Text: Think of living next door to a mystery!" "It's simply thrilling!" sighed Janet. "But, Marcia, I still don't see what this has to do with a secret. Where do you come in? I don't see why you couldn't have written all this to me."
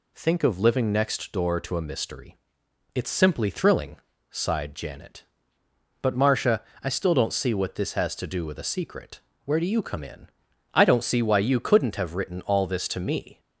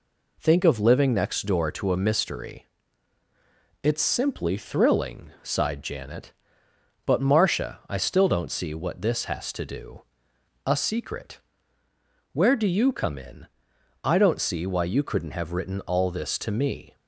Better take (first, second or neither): first